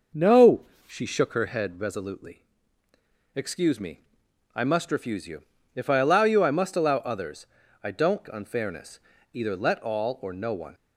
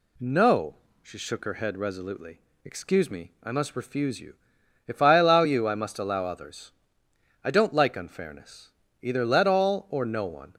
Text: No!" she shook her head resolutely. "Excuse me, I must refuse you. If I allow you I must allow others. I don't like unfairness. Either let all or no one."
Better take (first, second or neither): second